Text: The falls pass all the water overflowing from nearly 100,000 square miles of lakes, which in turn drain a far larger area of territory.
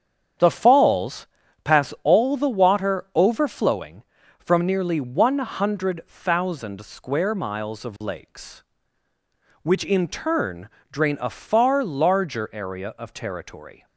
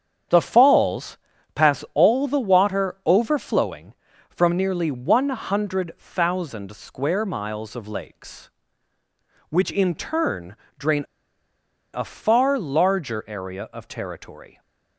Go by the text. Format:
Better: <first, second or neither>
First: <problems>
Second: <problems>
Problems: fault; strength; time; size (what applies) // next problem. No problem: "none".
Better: first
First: starts louder than the rest; strong; until 1.7 s; 8.5 dB // pauses between "falls" and "pass"; at 1.2 s; 0.38 s long // pauses between "turn" and "drain"; slight; at 10.6 s; 0.22 s long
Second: starts louder than the rest; strong; until 1.6 s; 8.5 dB // pauses between "falls" and "pass"; at 1.1 s; 0.38 s long // pauses between "turn" and "drain"; slight; at 10.5 s; 0.22 s long // pauses between "drain" and "a"; noticeable; at 11.0 s; 0.89 s long